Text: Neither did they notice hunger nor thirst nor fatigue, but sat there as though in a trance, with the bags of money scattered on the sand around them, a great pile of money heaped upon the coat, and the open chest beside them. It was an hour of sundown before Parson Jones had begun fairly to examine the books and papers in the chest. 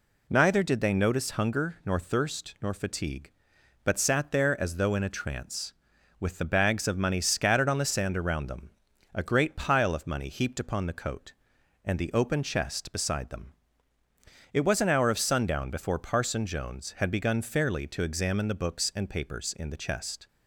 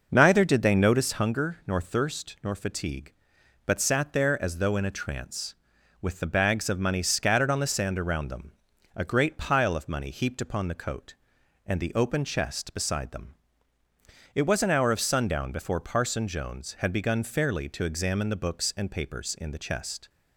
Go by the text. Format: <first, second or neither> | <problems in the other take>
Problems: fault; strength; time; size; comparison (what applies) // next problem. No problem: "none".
first | starts louder than the rest; noticeable; until 1.3 s; 5.5 dB